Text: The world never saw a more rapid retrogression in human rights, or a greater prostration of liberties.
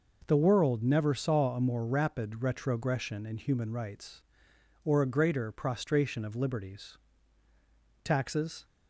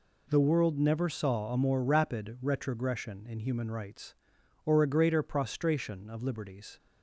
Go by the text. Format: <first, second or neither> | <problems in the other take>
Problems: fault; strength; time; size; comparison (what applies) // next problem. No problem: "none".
second | goes on to say "Taxes"; from 8.0 s on; 0.60 s long